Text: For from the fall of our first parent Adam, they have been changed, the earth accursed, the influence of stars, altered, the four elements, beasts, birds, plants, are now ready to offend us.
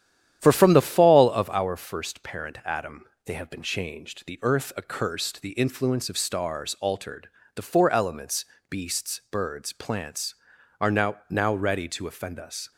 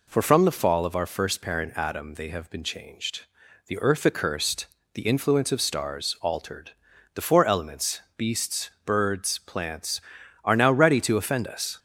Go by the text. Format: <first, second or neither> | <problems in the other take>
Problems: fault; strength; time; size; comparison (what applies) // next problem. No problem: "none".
second | starts louder than the rest; strong; until 1.4 s; 10.5 dB // says "now" twice; at 11.2 s